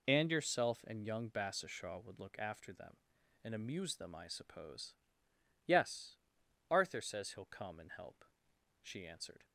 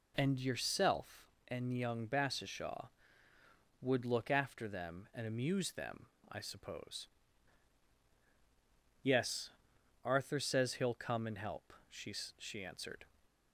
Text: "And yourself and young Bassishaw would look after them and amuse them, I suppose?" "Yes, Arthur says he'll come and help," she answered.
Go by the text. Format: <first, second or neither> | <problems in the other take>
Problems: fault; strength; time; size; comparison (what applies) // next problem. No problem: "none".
first | says "she" twice; at 12.3 s